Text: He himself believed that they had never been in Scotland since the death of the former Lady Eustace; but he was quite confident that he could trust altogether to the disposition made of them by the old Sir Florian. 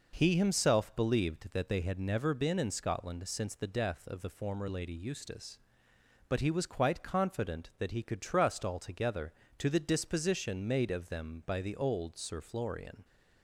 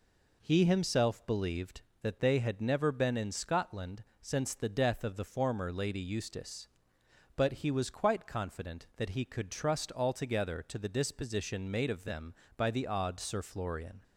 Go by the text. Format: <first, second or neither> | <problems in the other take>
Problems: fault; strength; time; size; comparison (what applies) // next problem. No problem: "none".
first | pauses between "Scotland" and "since"; slight; at 4.0 s; 0.16 s long // says "odd" for "old"; at 12.8 s